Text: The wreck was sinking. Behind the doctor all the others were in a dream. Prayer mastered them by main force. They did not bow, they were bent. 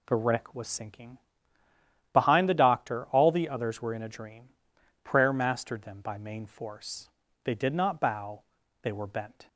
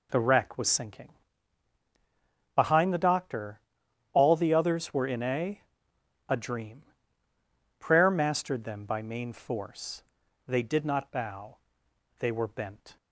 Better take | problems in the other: first | pauses between "doctor" and "all"; noticeable; at 3.6 s; 0.52 s long // says "a" twice; at 6.2 s

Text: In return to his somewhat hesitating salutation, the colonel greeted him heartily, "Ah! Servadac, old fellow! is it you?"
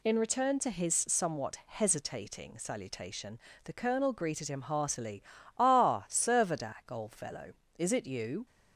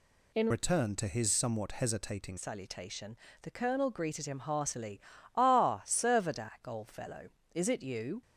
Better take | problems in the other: first | changes voice from "return" to "hesitating"; from 0.5 to 2.3 s; 1.8 s long

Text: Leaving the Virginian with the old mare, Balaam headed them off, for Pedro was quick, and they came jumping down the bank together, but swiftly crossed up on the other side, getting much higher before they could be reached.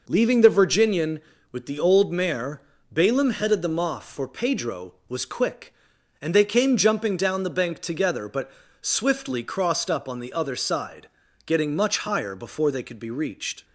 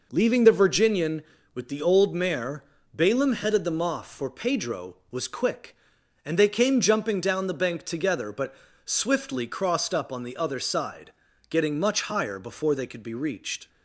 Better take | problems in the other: neither | pauses between "but" and "swiftly"; slight; the same in both

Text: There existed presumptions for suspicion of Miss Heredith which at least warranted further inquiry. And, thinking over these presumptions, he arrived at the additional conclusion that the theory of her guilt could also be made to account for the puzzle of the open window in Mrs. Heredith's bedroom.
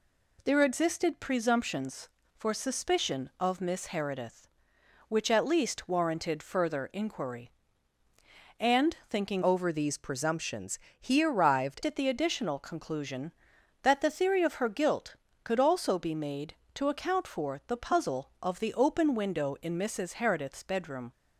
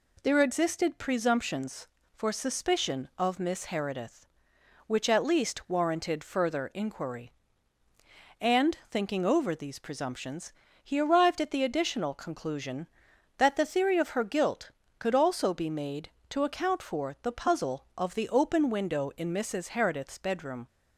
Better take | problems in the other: second | changes voice from "over" to "arrived"; from 9.4 to 11.8 s; 2.4 s long

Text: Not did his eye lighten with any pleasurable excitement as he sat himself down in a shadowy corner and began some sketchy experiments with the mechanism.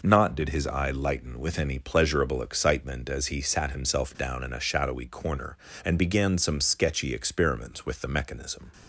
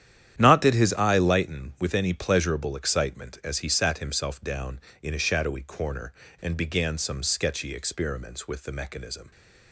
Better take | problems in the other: first | starts louder than the rest; strong; until 1.5 s; 10.5 dB

